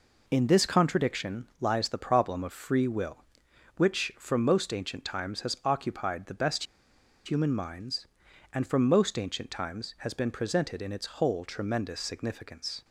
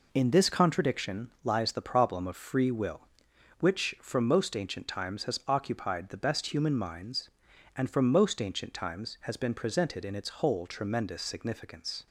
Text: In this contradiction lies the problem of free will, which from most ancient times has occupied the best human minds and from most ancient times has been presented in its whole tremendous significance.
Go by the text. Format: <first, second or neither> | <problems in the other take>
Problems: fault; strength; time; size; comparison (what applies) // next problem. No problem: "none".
second | pauses between "best" and "human"; noticeable; at 6.6 s; 0.61 s long